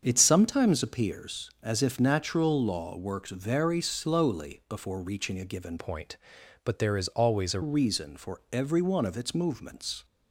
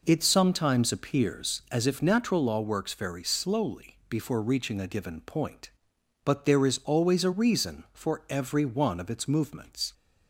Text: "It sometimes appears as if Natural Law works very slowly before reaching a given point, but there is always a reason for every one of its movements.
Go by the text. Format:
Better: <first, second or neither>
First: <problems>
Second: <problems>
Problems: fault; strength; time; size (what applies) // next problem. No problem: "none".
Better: second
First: starts louder than the rest; strong; until 1.0 s; 7 dB // changes voice from "point" to "a"; from 5.7 to 7.6 s; 1.9 s long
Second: none